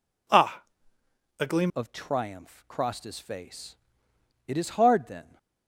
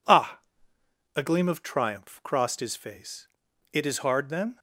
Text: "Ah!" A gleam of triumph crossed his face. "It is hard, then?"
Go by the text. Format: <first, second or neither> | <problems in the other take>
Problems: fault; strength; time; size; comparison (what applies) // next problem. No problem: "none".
second | changes voice at "of"; from 1.7 s on; 3.6 s long